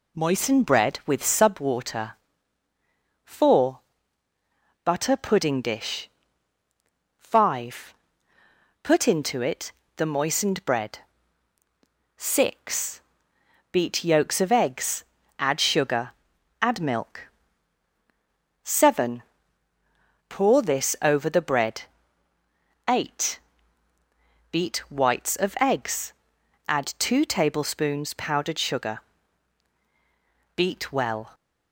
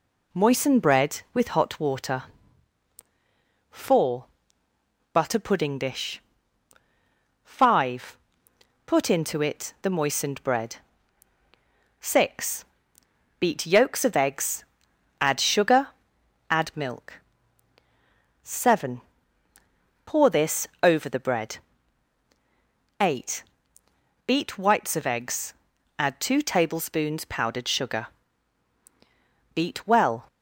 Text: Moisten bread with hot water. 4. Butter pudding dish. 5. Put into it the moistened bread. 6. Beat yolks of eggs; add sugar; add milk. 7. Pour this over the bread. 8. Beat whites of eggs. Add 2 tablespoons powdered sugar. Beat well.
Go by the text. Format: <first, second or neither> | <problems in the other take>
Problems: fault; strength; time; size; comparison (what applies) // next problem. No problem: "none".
second | says "sub" for "hot"; at 1.2 s // pauses between "it" and "the"; slight; at 9.7 s; 0.24 s long